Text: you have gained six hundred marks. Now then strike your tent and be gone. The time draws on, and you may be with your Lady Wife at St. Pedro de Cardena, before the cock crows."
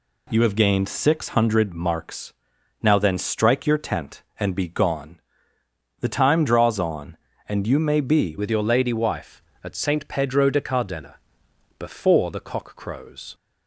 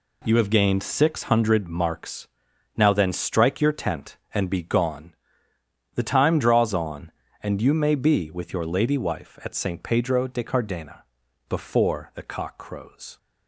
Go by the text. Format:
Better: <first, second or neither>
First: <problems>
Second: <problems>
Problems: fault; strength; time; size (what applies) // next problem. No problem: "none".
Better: second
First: changes voice at "with"; from 8.3 s on; 5.0 s long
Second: none